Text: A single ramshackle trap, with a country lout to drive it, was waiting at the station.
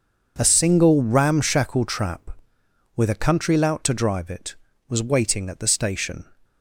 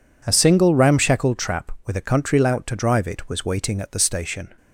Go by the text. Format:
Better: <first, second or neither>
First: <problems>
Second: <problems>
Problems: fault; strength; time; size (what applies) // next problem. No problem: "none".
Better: neither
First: none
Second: none